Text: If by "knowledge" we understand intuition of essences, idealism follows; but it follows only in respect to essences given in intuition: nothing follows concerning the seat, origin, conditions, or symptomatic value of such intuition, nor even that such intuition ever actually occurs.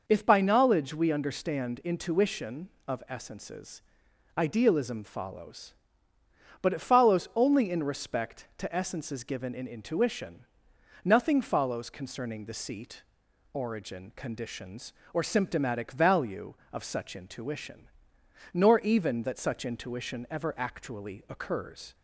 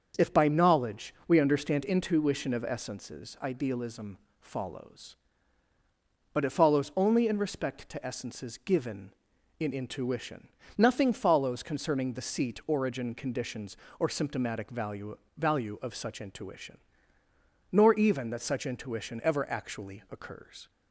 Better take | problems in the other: first | starts louder than the rest; until 1.3 s; 7 dB // pauses between "idealism" and "follows"; slight; at 4.1 s; 0.22 s long // says "value" twice; at 15.3 s

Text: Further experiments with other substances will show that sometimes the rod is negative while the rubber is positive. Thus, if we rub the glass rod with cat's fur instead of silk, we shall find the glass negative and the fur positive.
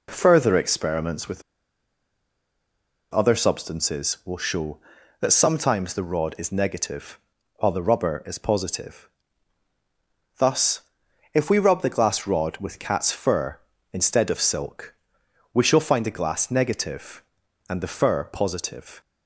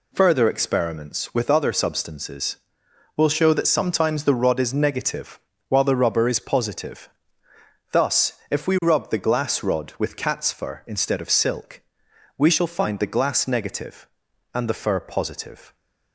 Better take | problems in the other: second | pauses between "with" and "other"; strong; at 1.4 s; 1.7 s long // pauses between "negative" and "while"; at 7.1 s; 0.40 s long; slight in the second

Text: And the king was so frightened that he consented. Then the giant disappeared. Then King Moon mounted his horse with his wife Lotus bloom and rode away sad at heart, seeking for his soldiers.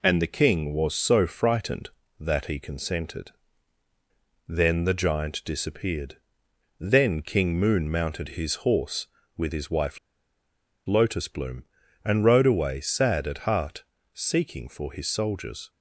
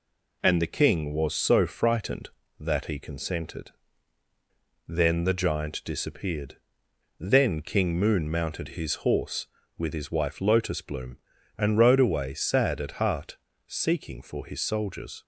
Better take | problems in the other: second | pauses between "wife" and "Lotus"; noticeable; at 9.9 s; 0.88 s long

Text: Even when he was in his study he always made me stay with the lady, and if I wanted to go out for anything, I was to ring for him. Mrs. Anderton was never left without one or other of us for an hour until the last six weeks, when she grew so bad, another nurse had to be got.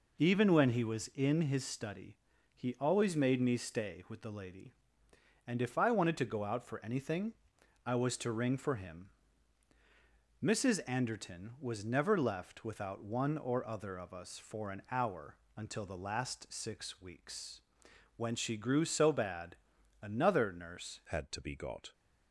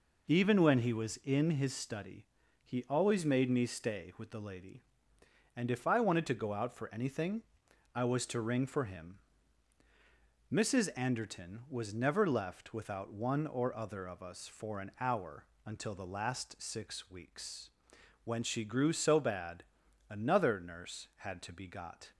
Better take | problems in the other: second | pauses between "study" and "he"; at 2.1 s; 0.40 s long; also in the second // pauses between "hour" and "until"; slight; at 15.3 s; 0.22 s long; slight in the second // changes voice at "had"; from 21.1 s on; 0.8 s long

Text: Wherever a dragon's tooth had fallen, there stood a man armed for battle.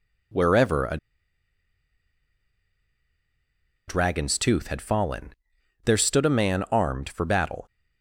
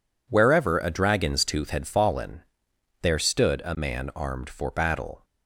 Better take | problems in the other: second | pauses between "a" and "dragon's"; strong; at 0.9 s; 2.9 s long

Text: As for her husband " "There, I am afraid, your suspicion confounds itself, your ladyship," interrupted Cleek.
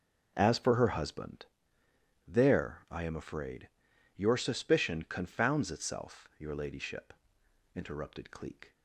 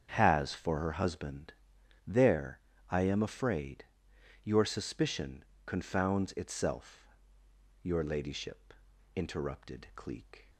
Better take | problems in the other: first | starts louder than the rest; strong; until 1.1 s; 7.5 dB // says "Has" for "As"; at 0.1 s // pauses between "suspicion" and "confounds"; slight; at 5.4 s; 0.22 s long

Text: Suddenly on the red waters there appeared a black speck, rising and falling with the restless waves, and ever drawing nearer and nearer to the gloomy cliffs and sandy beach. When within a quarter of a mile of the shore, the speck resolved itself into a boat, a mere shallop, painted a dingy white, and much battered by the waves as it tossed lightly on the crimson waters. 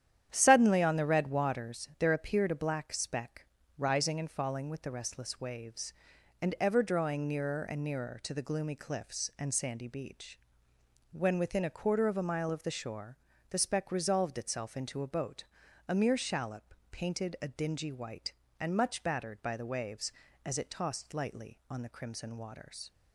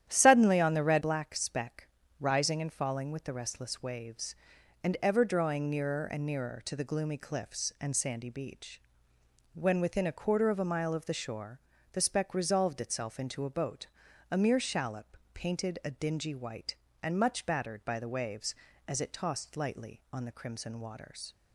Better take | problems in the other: first | starts louder than the rest; strong; until 1.1 s; 10.5 dB; strong in the first // skips "waters there appeared a"; at 1.0 s

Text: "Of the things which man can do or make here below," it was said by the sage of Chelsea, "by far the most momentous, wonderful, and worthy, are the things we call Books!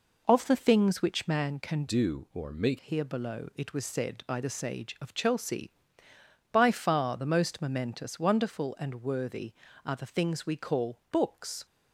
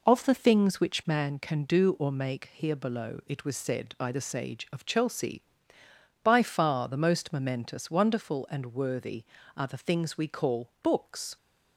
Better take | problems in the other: second | changes voice from "do" to "make"; from 1.8 to 2.7 s; 0.9 s long

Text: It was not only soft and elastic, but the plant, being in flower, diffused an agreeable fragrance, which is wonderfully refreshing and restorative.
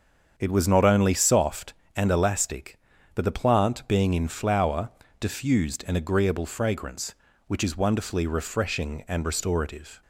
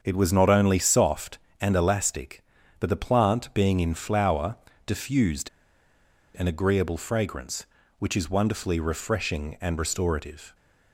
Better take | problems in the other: first | starts louder than the rest; until 1.0 s; 7 dB; also in the first // pauses between "diffused" and "an"; noticeable; at 5.4 s; 0.89 s long

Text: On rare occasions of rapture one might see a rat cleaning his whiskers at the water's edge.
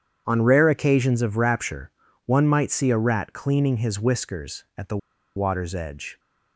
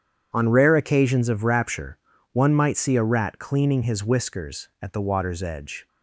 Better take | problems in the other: second | starts louder than the rest; strong; until 1.2 s; 8.5 dB; strong in the second // pauses between "rapture" and "one"; slight; at 1.9 s; 0.34 s long; slight in the second // pauses between "the" and "water's"; at 4.9 s; 0.39 s long

